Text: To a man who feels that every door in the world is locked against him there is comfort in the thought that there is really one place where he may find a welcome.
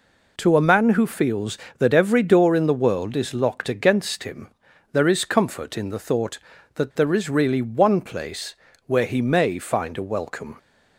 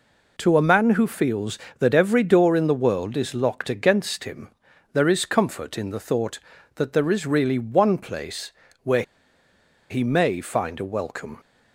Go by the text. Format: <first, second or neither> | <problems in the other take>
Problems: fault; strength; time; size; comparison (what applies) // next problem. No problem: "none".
first | pauses between "him" and "there"; at 4.5 s; 0.42 s long; also in the first // pauses between "place" and "where"; slight; at 8.5 s; 0.30 s long; slight in the first // pauses between "where" and "he"; noticeable; at 9.0 s; 0.87 s long